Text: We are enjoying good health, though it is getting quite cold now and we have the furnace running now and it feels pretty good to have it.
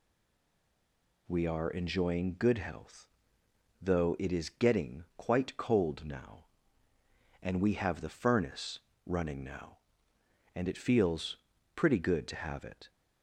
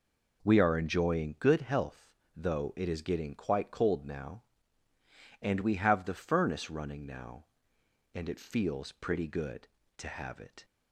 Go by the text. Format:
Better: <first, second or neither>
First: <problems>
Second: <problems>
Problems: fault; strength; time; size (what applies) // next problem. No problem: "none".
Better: second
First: stays silent before the first word; noticeable; until 1.2 s; 1.2 s long // pauses between "furnace" and "running"; slight; at 8.7 s; 0.26 s long // pauses between "feels" and "pretty"; at 11.3 s; 0.38 s long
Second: none